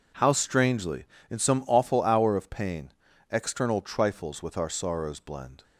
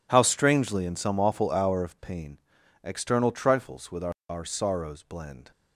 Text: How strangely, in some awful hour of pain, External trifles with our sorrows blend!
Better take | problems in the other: first | says "our" twice; at 4.2 s

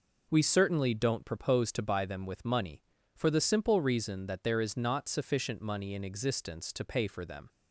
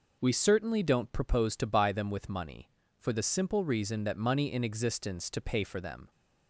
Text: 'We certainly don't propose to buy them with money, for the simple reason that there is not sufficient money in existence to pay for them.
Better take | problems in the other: first | skips "there is not sufficient"; at 4.1 s

